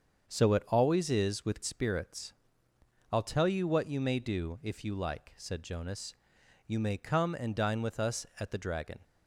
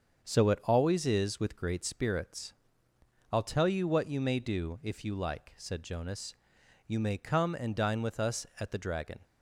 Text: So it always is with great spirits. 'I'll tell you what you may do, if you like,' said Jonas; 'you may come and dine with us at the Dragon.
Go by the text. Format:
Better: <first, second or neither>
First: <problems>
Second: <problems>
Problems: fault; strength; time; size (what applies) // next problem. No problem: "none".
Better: second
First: starts louder than the rest; until 1.3 s; 7 dB // skips "great"; at 1.6 s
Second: starts louder than the rest; until 1.2 s; 7 dB